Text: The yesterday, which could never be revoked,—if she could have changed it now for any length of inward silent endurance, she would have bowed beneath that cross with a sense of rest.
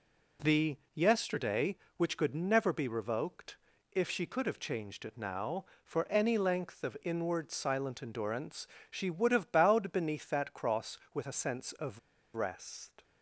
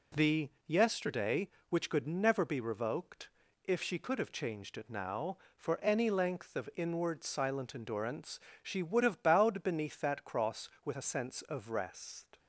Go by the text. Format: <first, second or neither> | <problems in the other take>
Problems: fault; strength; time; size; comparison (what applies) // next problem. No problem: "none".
second | pauses between "The" and "yesterday"; slight; at 0.7 s; 0.18 s long; slight in the second // pauses between "of" and "rest"; slight; at 11.9 s; 0.35 s long